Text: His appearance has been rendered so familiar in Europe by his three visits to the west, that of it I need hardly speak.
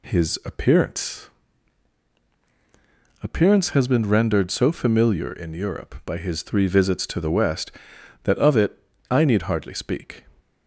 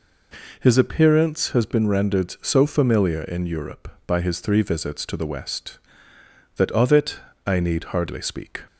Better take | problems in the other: second | says "appearance" twice; at 3.2 s // pauses between "it" and "I"; slight; at 8.7 s; 0.32 s long; slight in the second

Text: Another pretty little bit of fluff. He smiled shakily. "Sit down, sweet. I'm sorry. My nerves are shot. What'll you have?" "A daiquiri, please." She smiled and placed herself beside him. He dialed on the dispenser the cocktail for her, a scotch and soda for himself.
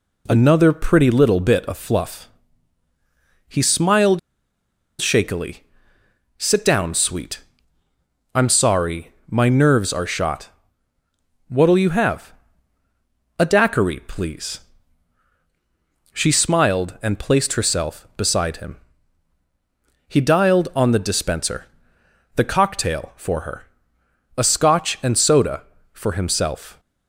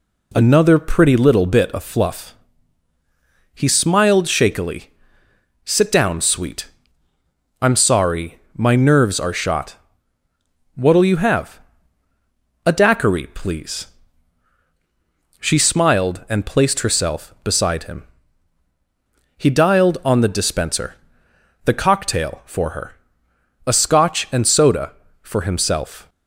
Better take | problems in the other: second | pauses between "smiled" and "shakily"; noticeable; at 4.1 s; 0.79 s long // pauses between "dispenser" and "the"; noticeable; at 21.6 s; 0.68 s long; noticeable in the second

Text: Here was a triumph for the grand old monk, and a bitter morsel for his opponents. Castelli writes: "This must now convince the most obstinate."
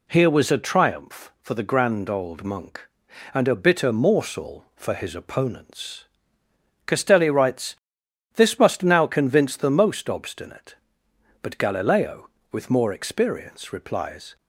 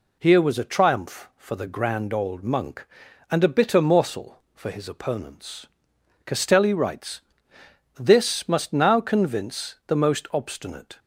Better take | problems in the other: second | goes on to say "But Galileo with more experience replies"; strong; from 11.4 s on; 2.9 s long

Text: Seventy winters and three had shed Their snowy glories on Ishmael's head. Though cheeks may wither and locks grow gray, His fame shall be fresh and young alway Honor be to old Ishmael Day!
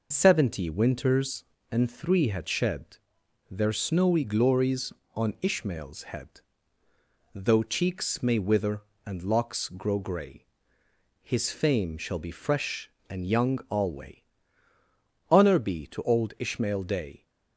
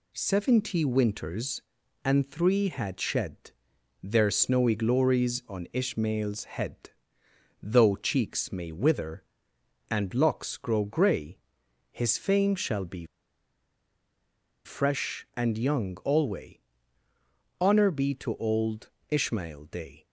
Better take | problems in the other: first | pauses between "shed" and "Their"; noticeable; at 3.5 s; 0.50 s long; noticeable in the first // pauses between "be" and "fresh"; strong; at 13.0 s; 1.5 s long // pauses between "alway" and "Honor"; at 16.5 s; 1.0 s long; also in the first // pauses between "old" and "Ishmael"; slight; at 18.9 s; 0.18 s long

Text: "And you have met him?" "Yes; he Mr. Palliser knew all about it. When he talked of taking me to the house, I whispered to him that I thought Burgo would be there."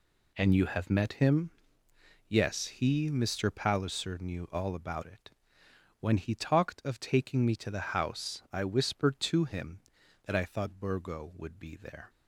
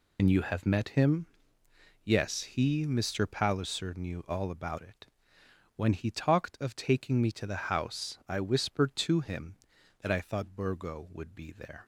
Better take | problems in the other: first | loses the start of "And"; at 0.1 s; 85 ms

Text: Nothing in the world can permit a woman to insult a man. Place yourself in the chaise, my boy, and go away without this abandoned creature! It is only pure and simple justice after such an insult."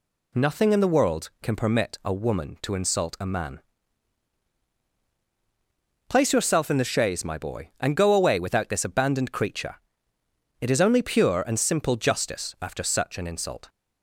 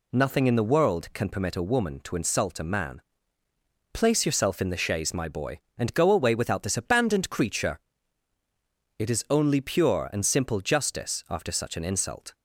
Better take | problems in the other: neither | none

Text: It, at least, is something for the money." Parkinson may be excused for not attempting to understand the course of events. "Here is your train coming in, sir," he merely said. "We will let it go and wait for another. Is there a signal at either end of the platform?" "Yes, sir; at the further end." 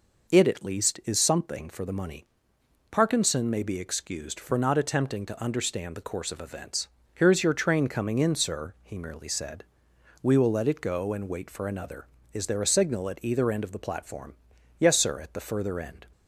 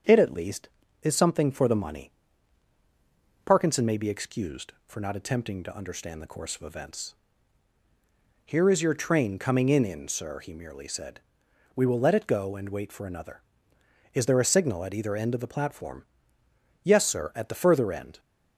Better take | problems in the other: first | starts louder than the rest; strong; until 1.3 s; 7 dB // says "in" twice; at 9.8 s

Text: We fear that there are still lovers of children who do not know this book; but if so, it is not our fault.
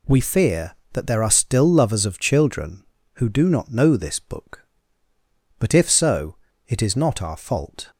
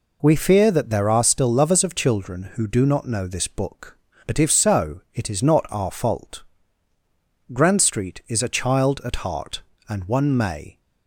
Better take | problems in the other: first | goes on to say "Grand Street is a child at heart and one may"; strong; from 7.5 s on; 3.2 s long

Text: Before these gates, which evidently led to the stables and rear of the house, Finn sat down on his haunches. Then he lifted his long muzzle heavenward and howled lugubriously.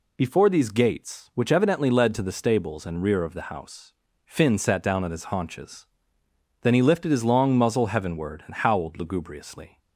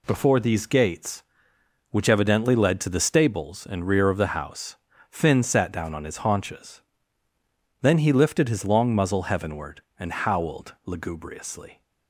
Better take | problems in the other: neither | none

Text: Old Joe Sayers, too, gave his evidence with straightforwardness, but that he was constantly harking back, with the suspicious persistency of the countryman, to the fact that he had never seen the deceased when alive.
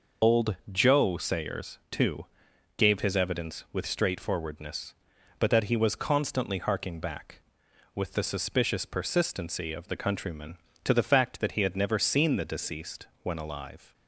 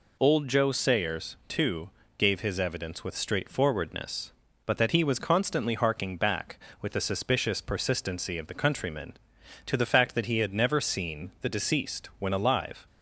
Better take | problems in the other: second | loses the start of "Old"; at 0.2 s; 50 ms // pauses between "Old" and "Joe"; slight; at 0.5 s; 0.16 s long // pauses between "deceased" and "when"; slight; at 13.0 s; 0.16 s long

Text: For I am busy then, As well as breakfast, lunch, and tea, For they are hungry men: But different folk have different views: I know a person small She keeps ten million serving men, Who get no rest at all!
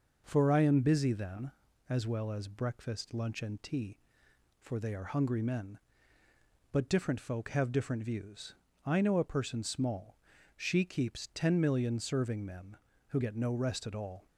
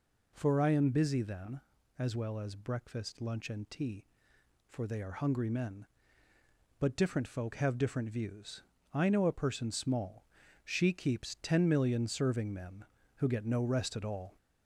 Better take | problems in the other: first | gets louder; slight; throughout; 2.5 dB // pauses between "small" and "She"; at 10.2 s; 0.40 s long; also in the first

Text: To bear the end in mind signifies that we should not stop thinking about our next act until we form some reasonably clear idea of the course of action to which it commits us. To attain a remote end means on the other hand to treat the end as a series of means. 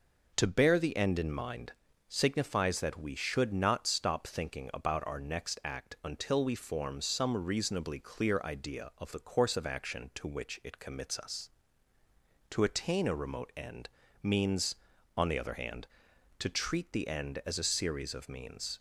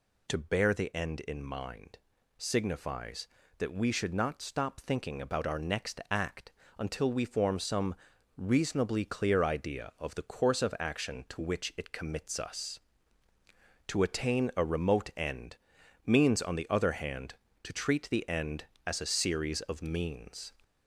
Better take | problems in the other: first | gets louder; throughout; 3.5 dB // pauses between "mind" and "signifies"; at 1.9 s; 0.38 s long; slight in the first // pauses between "act" and "until"; slight; at 6.5 s; 0.28 s long // pauses between "some" and "reasonably"; at 7.9 s; 0.42 s long // pauses between "end" and "means"; noticeable; at 15.5 s; 0.48 s long; slight in the first

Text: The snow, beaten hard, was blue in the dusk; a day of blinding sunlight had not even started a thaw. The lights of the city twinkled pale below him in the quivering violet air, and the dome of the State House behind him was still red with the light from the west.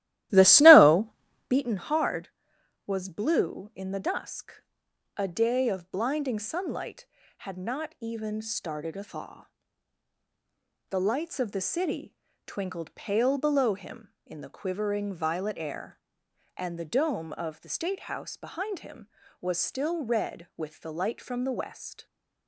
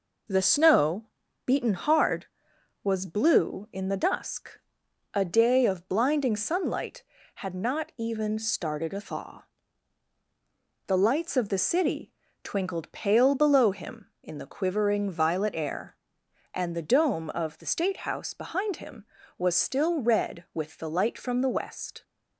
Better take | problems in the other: second | starts louder than the rest; strong; until 1.6 s; 15 dB // pauses between "city" and "twinkled"; slight; at 12.1 s; 0.32 s long; slight in the second

